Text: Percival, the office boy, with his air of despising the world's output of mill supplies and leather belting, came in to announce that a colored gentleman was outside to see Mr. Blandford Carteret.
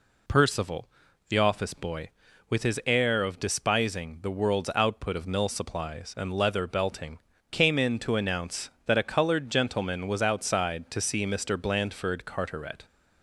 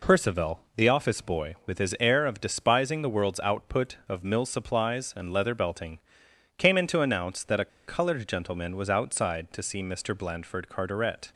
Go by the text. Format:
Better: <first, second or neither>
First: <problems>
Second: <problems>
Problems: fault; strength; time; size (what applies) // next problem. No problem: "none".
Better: first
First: none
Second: pauses between "a" and "colored"; slight; at 7.6 s; 0.18 s long